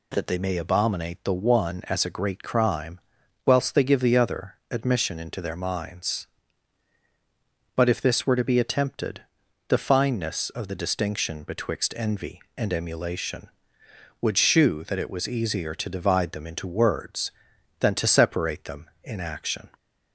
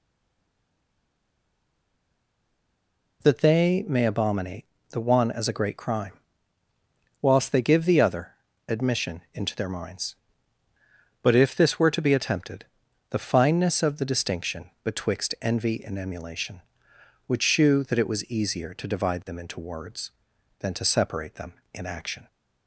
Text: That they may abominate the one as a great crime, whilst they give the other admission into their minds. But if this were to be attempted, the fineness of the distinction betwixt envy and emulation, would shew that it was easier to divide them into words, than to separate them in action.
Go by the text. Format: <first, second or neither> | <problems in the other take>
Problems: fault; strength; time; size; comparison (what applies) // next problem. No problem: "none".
first | stays silent before the first word; strong; until 3.2 s; 3.2 s long // pauses between "abominate" and "the"; slight; at 4.6 s; 0.26 s long // pauses between "other" and "admission"; slight; at 8.3 s; 0.36 s long